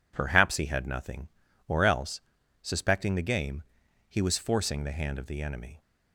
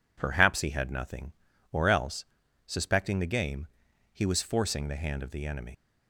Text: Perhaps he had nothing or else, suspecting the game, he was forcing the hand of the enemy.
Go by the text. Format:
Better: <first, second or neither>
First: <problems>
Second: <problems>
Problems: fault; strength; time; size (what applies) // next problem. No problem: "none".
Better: first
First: none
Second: leaves "enemy" unfinished; at 5.7 s; 95 ms